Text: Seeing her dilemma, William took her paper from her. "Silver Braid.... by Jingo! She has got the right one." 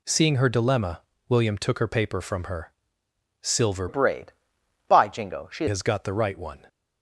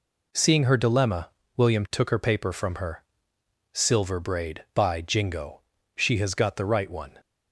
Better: second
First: changes voice from "Braid" to "She"; from 3.8 to 5.6 s; 1.8 s long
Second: none

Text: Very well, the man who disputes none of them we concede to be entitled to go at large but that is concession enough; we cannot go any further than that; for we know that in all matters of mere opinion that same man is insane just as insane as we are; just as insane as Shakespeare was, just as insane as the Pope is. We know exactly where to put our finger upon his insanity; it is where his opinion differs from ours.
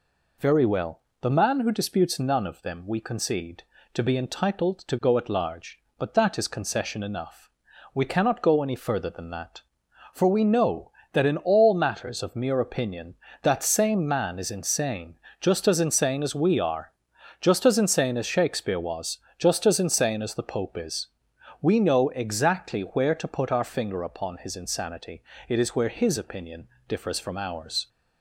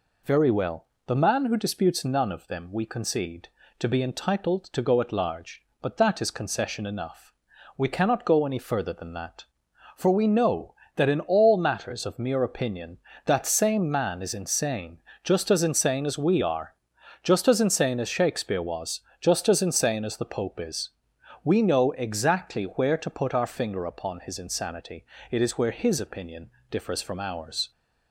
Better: neither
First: pauses between "insane" and "just"; slight; at 15.1 s; 0.22 s long // pauses between "opinion" and "differs"; slight; at 26.6 s; 0.22 s long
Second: pauses between "insane" and "just"; slight; at 15.0 s; 0.22 s long // pauses between "opinion" and "differs"; slight; at 26.4 s; 0.22 s long

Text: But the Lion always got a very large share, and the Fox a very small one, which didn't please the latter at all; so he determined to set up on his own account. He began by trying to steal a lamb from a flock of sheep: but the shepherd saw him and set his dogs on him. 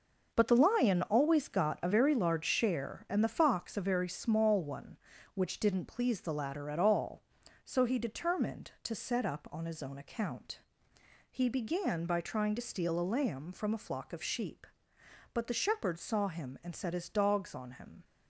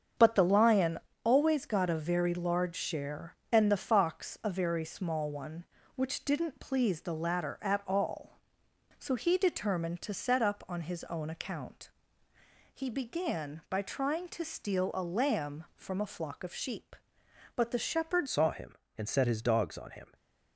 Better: first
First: none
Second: starts louder than the rest; strong; until 1.4 s; 7.5 dB // pauses between "Lion" and "always"; slight; at 0.9 s; 0.24 s long // changes voice at "saw"; from 18.2 s on; 1.9 s long // stays silent after the last word; slight; from 20.0 s on; 0.5 s long

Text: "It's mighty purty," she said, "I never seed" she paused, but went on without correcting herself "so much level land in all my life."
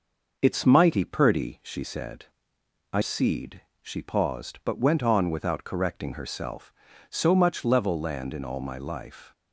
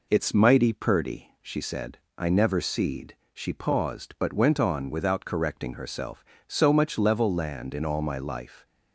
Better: second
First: skips "never"; at 3.0 s // pauses between "seed" and "she"; slight; at 3.6 s; 0.18 s long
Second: pauses between "seed" and "she"; slight; at 3.1 s; 0.16 s long

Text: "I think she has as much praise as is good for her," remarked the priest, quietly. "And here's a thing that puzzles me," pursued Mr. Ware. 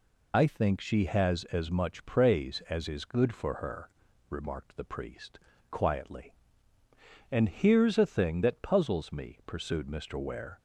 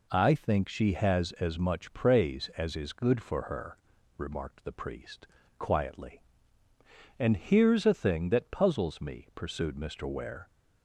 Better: second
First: loses the start of "I"; at 0.3 s; 125 ms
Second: none

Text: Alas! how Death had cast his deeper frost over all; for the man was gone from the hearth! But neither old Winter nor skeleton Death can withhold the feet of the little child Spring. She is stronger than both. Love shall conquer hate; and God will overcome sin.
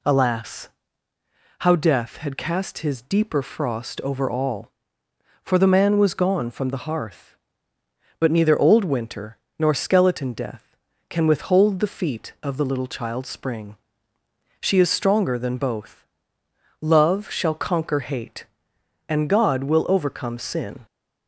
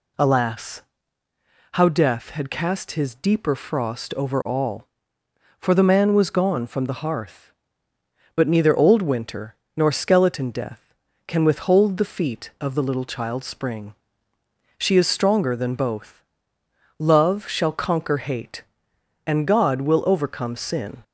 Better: neither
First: pauses between "Winter" and "nor"; slight; at 9.3 s; 0.22 s long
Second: pauses between "Winter" and "nor"; slight; at 9.5 s; 0.22 s long

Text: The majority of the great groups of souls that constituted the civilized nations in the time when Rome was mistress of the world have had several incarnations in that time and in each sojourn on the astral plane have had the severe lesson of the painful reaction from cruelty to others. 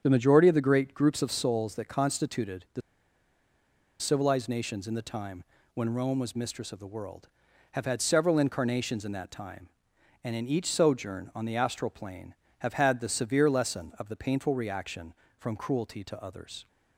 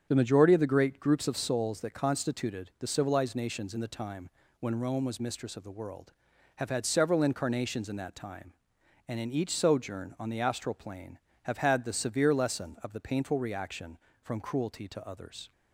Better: second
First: starts louder than the rest; strong; until 1.0 s; 8 dB // pauses between "the" and "civilized"; at 2.8 s; 1.2 s long // pauses between "time" and "when"; slight; at 5.4 s; 0.30 s long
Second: starts louder than the rest; strong; until 1.1 s; 8 dB // pauses between "time" and "when"; slight; at 4.2 s; 0.30 s long

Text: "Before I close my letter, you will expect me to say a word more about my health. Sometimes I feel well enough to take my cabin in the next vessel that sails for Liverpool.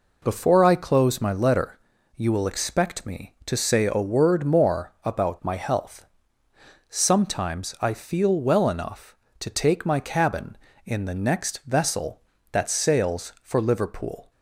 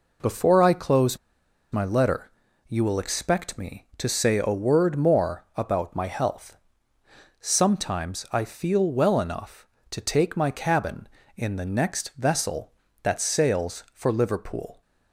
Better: first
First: none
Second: pauses between "close" and "my"; noticeable; at 1.1 s; 0.54 s long

